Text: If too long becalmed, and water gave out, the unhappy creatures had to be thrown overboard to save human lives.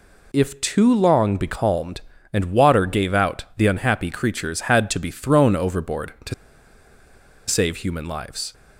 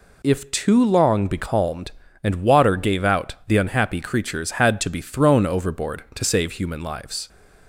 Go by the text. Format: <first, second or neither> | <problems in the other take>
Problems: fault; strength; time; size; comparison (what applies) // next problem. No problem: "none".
second | pauses between "to" and "save"; at 6.3 s; 1.1 s long